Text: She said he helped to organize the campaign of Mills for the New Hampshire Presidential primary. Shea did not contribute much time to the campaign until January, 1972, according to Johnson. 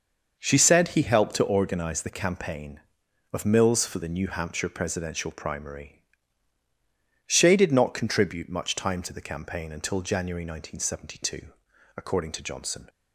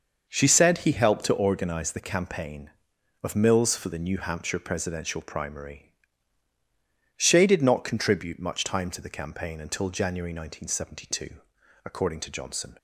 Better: neither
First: starts louder than the rest; noticeable; until 1.4 s; 6 dB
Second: starts louder than the rest; noticeable; until 1.2 s; 6 dB

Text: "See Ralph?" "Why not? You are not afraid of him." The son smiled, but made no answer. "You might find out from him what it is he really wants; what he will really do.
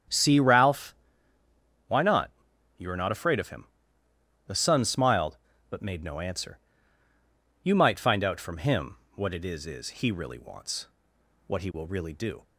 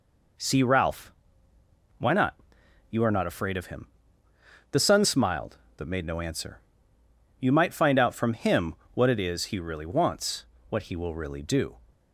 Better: second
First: starts louder than the rest; strong; until 2.0 s; 9 dB // pauses between "him" and "what"; slight; at 8.9 s; 0.20 s long // says "is" twice; at 9.6 s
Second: pauses between "him" and "what"; slight; at 8.7 s; 0.20 s long

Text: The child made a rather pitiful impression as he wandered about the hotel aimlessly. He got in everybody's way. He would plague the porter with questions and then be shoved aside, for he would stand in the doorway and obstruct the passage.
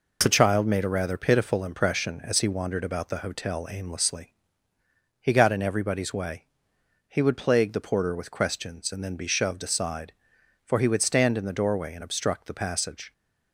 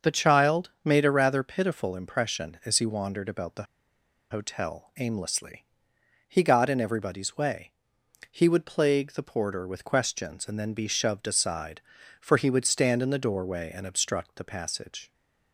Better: first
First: none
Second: starts louder than the rest; until 1.1 s; 6.5 dB // pauses between "the" and "hotel"; noticeable; at 3.6 s; 0.66 s long

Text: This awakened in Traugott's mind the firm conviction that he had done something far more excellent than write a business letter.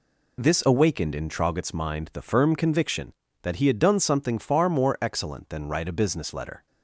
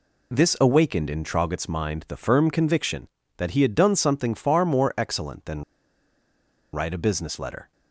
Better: first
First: none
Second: pauses between "than" and "write"; at 5.6 s; 1.1 s long

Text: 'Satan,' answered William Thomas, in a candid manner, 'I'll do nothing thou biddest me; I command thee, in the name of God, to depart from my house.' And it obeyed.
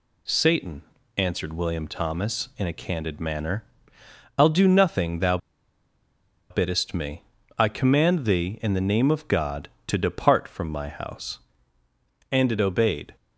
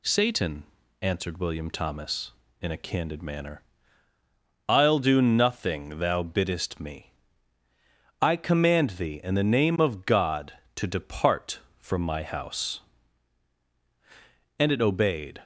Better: second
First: pauses between "thou" and "biddest"; at 5.3 s; 1.1 s long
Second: none

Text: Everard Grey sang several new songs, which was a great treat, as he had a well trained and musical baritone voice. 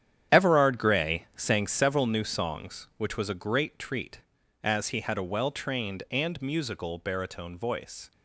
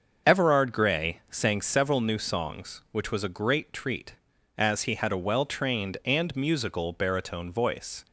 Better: second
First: gets quieter; strong; throughout; 11 dB // starts louder than the rest; strong; until 1.4 s; 9.5 dB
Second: starts louder than the rest; until 1.3 s; 6.5 dB

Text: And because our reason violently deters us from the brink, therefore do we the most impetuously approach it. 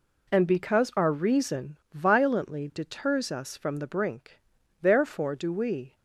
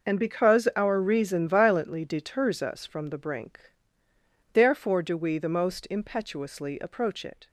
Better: second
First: pauses between "reason" and "violently"; slight; at 1.7 s; 0.16 s long // stops before "the most impetuously approach it"; at 5.9 s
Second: none

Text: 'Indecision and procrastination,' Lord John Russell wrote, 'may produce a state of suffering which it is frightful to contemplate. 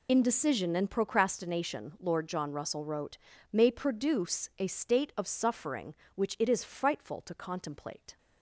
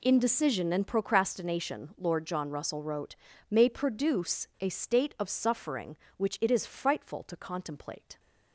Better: second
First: loses the start of "Indecision"; at 0.0 s; 40 ms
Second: none

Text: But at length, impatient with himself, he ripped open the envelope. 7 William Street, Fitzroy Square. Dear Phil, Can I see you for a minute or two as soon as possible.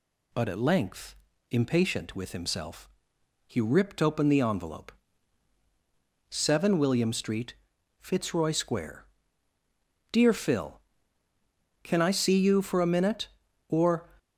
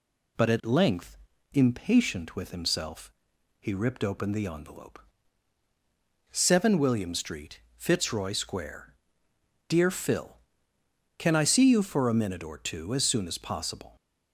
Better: second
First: stops before "two as soon as possible"; at 14.1 s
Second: none

